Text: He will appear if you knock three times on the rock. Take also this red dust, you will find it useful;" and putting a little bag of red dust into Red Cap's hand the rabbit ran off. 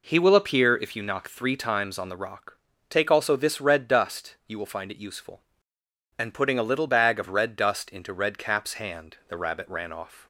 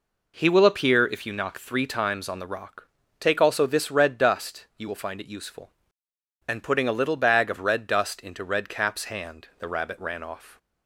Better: neither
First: none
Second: none

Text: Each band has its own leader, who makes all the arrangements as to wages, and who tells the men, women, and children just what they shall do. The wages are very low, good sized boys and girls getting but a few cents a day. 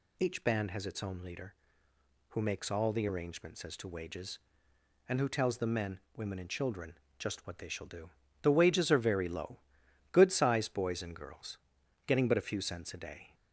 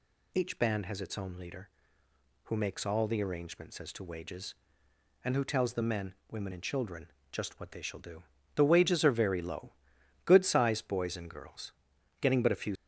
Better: first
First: pauses between "children" and "just"; slight; at 6.9 s; 0.20 s long // pauses between "girls" and "getting"; noticeable; at 11.5 s; 0.50 s long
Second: pauses between "children" and "just"; slight; at 7.1 s; 0.20 s long // pauses between "girls" and "getting"; noticeable; at 11.7 s; 0.50 s long // stops before "cents a day"; at 12.7 s

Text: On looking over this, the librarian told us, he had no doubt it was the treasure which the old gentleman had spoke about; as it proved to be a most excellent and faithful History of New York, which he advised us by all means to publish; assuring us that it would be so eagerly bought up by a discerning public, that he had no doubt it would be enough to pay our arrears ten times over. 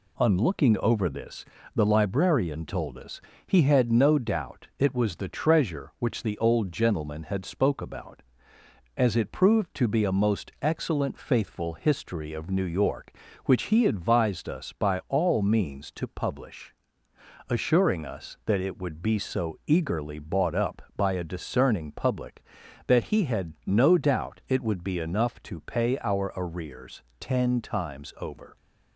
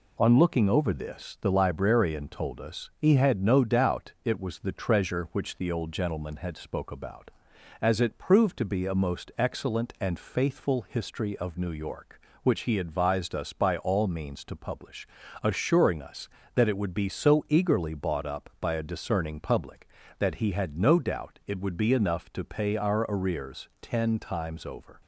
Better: second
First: skips "and"; at 11.1 s // pauses between "arrears" and "ten"; slight; at 27.0 s; 0.18 s long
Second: none

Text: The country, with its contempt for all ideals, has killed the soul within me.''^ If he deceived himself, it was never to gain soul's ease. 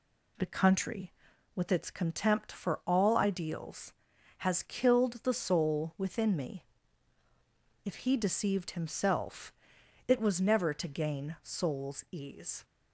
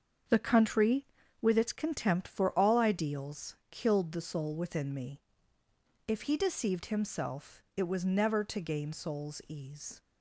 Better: first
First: none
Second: starts louder than the rest; until 1.6 s; 7 dB // skips "has"; at 3.6 s

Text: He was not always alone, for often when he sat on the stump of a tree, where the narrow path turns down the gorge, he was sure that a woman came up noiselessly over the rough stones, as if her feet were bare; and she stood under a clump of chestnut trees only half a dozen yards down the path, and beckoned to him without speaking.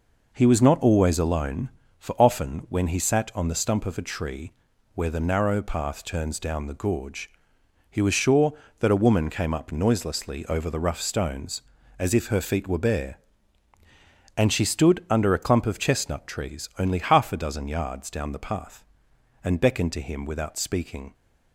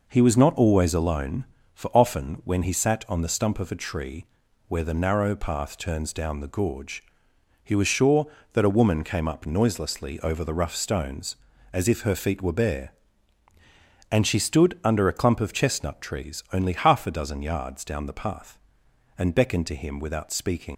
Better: first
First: none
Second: leaves "speaking" unfinished; at 20.7 s; 120 ms

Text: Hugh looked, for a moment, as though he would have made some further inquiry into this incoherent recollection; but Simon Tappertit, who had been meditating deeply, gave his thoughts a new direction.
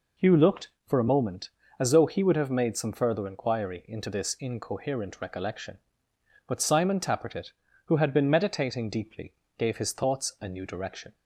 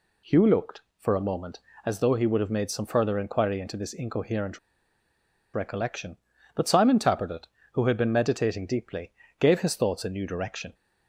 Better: first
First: none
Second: pauses between "incoherent" and "recollection"; noticeable; at 4.5 s; 0.96 s long

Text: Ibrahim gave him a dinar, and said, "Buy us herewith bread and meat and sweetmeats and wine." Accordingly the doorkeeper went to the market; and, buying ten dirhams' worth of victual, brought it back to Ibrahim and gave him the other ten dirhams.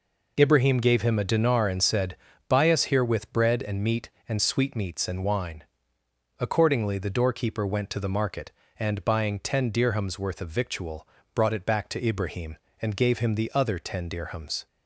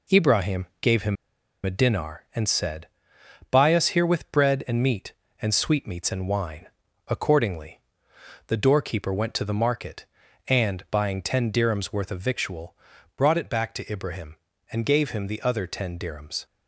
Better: first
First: none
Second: pauses between "him" and "a"; noticeable; at 1.1 s; 0.49 s long // pauses between "Accordingly" and "the"; noticeable; at 7.7 s; 0.68 s long

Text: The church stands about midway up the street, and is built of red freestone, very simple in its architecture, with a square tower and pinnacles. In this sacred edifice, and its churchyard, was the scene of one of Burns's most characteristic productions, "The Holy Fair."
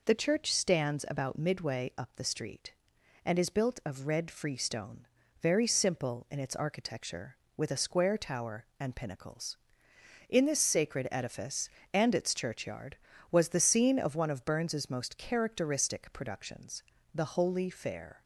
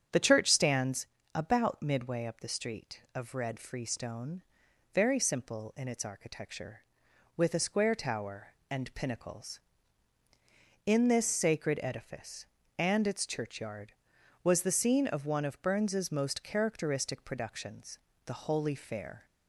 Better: first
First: none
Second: starts louder than the rest; strong; until 1.4 s; 8 dB // pauses between "stands" and "about"; slight; at 1.0 s; 0.30 s long // skips "and is built"; at 3.0 s

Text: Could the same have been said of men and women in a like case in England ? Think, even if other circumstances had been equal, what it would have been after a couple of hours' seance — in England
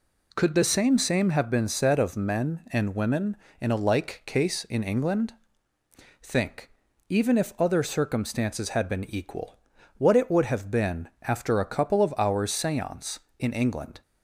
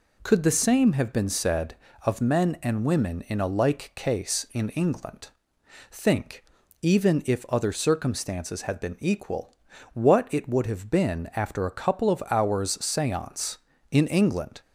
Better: second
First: says "same" twice; at 0.9 s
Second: none

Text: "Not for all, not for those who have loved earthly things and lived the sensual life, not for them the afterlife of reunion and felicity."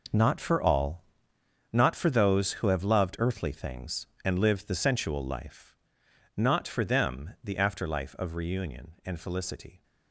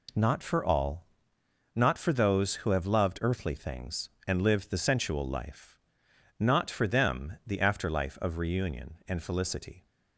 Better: second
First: gets quieter; strong; throughout; 12 dB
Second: none

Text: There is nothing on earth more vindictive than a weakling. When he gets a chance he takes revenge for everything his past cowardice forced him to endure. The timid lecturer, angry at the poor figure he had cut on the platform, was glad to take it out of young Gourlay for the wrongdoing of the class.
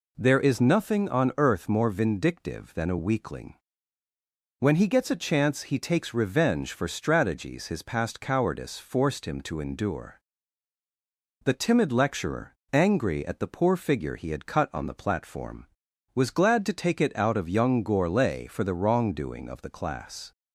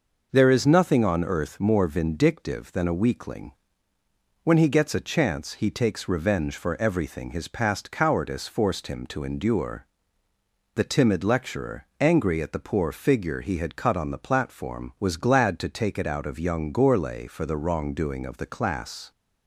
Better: second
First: says "strategies" for "everything"; at 6.8 s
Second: none

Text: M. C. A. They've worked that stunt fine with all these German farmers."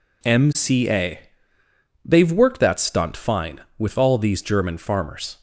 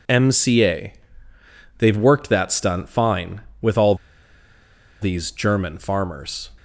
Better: first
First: pauses between "A" and "They've"; noticeable; at 1.1 s; 0.86 s long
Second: pauses between "A" and "They've"; noticeable; at 0.9 s; 0.86 s long // pauses between "all" and "these"; at 3.9 s; 1.0 s long

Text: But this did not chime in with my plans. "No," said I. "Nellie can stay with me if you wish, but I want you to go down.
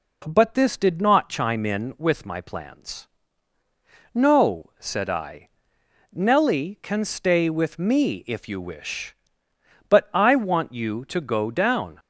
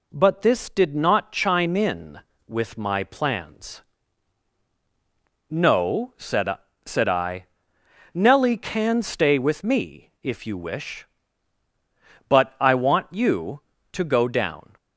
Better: first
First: none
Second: says "said" twice; at 6.8 s

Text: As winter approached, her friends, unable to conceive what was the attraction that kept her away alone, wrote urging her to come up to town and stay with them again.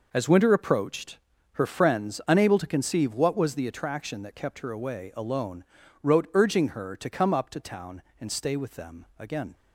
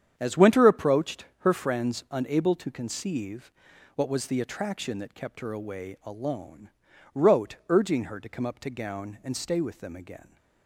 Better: first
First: none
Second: starts louder than the rest; strong; until 1.1 s; 8.5 dB // pauses between "conceive" and "what"; at 3.5 s; 0.44 s long // says "gown" for "town"; at 8.7 s

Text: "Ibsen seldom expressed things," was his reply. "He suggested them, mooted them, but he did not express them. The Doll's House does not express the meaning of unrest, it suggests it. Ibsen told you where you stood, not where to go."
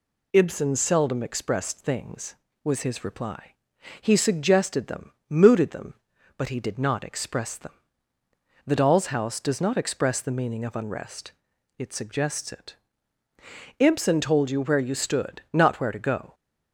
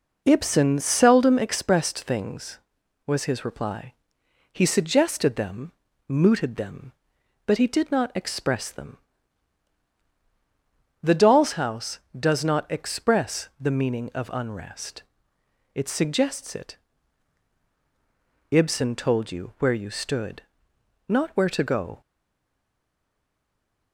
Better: first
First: none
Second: stays silent after the last word; noticeable; from 22.0 s on; 1.9 s long

